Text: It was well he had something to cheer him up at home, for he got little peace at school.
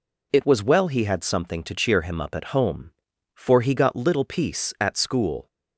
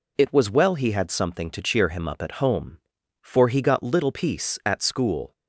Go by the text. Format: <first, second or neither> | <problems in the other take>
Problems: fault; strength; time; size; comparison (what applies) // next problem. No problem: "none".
neither | none